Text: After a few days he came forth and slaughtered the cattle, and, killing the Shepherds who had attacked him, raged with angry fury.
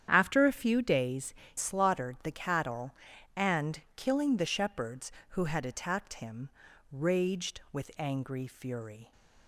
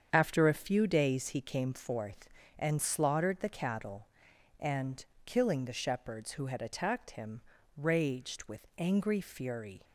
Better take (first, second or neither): second